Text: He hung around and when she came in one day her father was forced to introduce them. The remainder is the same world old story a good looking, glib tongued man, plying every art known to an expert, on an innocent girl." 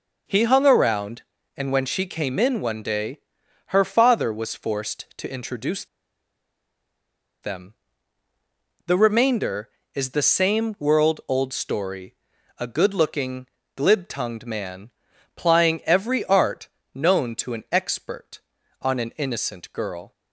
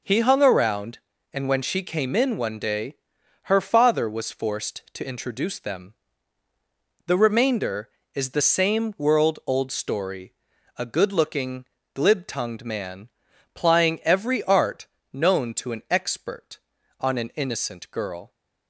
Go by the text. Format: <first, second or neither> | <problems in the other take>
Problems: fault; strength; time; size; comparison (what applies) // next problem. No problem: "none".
second | pauses between "day" and "her"; noticeable; at 3.1 s; 0.48 s long; noticeable in the second // pauses between "introduce" and "them"; strong; at 5.8 s; 1.5 s long // pauses between "story" and "a"; noticeable; at 12.1 s; 0.46 s long; noticeable in the second // pauses between "art" and "known"; slight; at 16.6 s; 0.26 s long; slight in the second